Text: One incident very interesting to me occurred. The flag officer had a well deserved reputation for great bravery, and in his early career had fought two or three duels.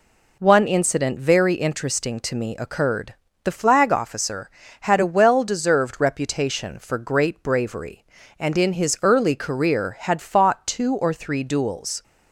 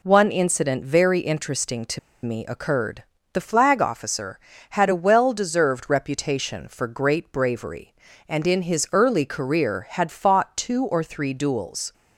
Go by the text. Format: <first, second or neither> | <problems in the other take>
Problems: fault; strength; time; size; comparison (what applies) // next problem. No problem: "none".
first | pauses between "to" and "me"; slight; at 1.9 s; 0.25 s long